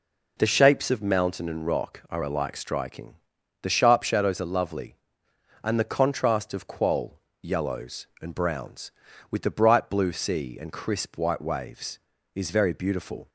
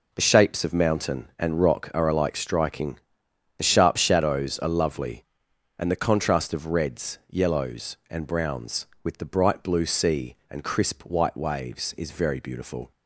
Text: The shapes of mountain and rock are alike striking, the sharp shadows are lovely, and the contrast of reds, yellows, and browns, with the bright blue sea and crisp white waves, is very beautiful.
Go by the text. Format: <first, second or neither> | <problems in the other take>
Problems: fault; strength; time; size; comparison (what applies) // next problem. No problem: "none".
second | says "qual" for "reds"; at 6.6 s